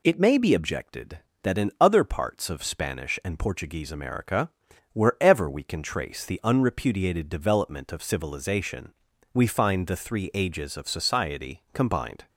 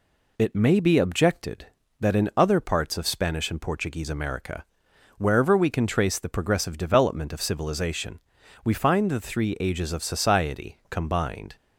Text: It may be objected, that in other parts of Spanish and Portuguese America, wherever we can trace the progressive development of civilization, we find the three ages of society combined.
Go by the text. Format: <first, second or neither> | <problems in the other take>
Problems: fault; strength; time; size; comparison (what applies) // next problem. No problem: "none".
second | says "unrepudiated" for "progressive"; at 6.4 s